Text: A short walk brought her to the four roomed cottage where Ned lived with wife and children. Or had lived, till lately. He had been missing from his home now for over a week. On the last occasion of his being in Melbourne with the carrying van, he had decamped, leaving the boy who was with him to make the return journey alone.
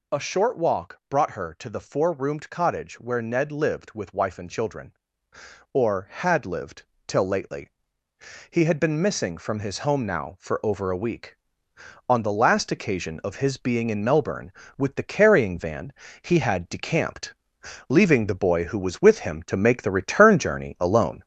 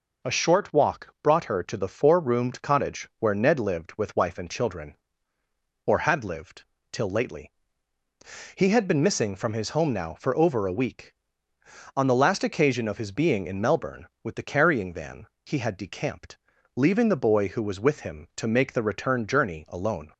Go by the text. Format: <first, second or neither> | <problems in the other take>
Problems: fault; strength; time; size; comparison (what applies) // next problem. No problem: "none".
second | gets louder; noticeable; throughout; 4.5 dB